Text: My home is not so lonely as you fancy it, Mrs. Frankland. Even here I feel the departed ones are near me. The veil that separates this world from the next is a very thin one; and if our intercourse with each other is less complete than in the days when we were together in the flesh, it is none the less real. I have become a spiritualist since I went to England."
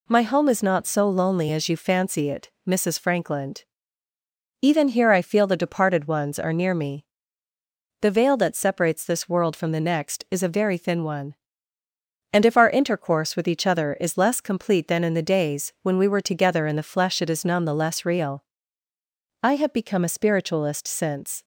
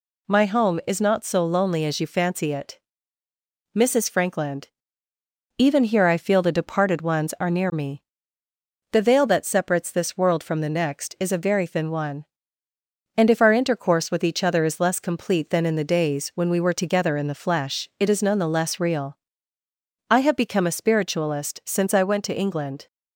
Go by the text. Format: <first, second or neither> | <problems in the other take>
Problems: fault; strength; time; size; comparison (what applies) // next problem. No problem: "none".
second | stops before "I went to England"; at 21.4 s